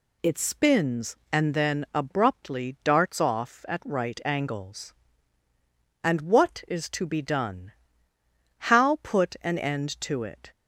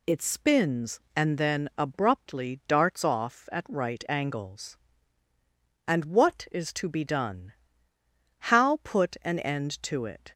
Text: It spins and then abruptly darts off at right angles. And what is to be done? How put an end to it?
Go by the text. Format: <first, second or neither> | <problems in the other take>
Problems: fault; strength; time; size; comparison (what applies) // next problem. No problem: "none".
neither | none